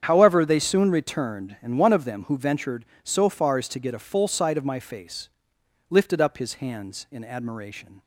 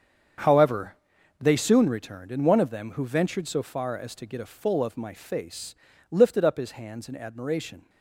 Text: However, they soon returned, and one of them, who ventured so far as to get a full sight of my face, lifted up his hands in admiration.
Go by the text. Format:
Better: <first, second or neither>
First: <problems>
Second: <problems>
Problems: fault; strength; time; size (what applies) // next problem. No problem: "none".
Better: first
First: starts louder than the rest; strong; until 1.0 s; 8.5 dB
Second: starts louder than the rest; strong; until 1.8 s; 7.5 dB // skips "sight"; at 4.8 s